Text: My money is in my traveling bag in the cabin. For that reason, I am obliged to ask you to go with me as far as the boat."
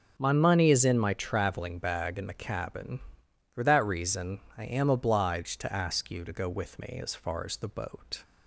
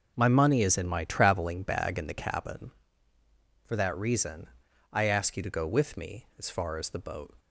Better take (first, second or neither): first